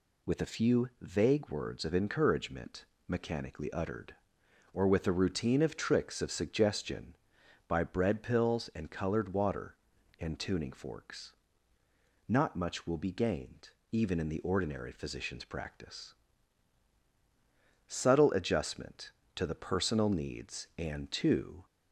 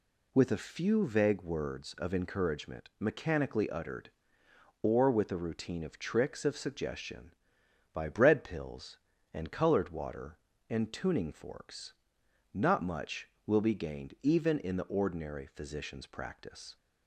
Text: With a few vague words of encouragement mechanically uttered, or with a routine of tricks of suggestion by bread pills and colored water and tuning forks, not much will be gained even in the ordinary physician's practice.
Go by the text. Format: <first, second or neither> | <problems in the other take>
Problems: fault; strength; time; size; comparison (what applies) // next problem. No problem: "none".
second | pauses between "encouragement" and "mechanically"; slight; at 2.8 s; 0.22 s long // pauses between "gained" and "even"; slight; at 13.7 s; 0.20 s long // goes on to say "Subtle adjustment to the personal needs and to"; strong; from 17.8 s on; 3.7 s long